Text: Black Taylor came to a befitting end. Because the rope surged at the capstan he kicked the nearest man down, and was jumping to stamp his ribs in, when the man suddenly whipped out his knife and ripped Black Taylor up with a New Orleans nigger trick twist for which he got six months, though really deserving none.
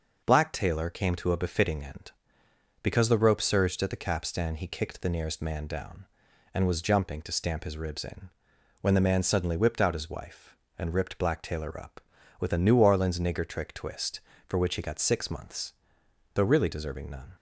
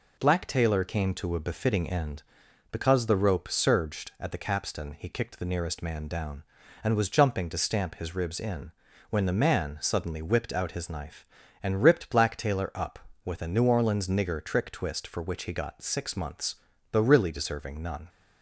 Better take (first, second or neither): second